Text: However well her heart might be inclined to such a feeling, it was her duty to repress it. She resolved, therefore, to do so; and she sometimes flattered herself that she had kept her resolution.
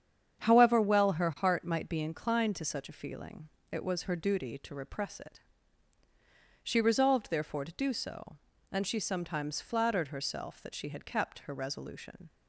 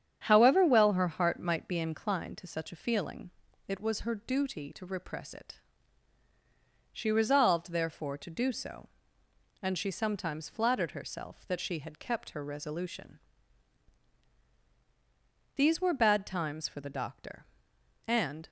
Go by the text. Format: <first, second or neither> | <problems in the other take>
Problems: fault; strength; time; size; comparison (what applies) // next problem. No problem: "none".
first | starts louder than the rest; strong; until 1.2 s; 8.5 dB; strong in the first // goes on to say "These were bad times for the doctor and"; strong; from 15.5 s on; 2.9 s long